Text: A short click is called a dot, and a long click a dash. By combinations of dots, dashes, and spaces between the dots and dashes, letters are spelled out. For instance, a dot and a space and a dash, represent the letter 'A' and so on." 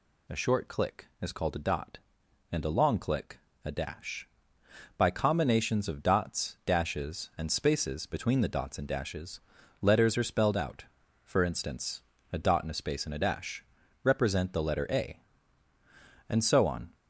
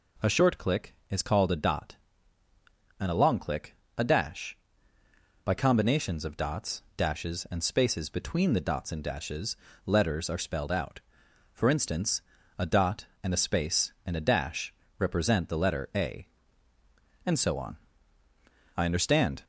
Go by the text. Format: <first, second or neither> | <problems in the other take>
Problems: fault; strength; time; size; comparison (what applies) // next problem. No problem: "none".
first | pauses between "click" and "a"; slight; at 3.7 s; 0.20 s long; slight in the first // goes on to say "I understand"; noticeable; from 18.7 s on; 0.68 s long